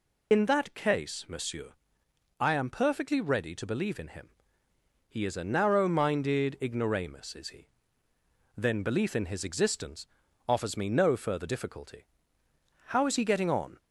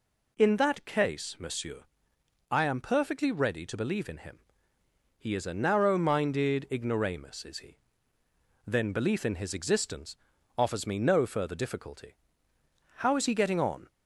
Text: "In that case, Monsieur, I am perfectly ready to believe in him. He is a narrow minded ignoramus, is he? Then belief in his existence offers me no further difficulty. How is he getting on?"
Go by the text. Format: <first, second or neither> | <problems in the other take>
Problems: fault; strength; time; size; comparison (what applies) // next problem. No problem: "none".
second | loses the start of "In"; at 0.3 s; 55 ms // pauses between "existence" and "offers"; at 10.0 s; 0.42 s long; also in the second